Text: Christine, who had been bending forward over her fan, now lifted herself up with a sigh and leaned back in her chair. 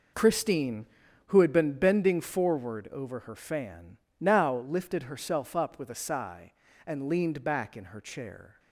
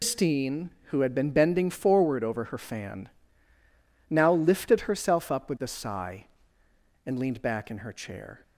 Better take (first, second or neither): first